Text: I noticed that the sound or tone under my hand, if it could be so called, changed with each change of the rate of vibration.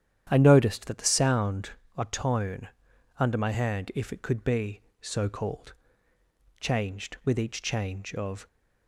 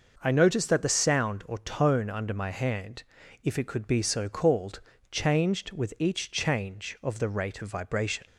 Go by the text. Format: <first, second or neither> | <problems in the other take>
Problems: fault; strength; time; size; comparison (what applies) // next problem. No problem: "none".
second | starts louder than the rest; strong; until 1.3 s; 10 dB // pauses between "tone" and "under"; noticeable; at 2.6 s; 0.50 s long // stops before "the rate of vibration"; at 8.4 s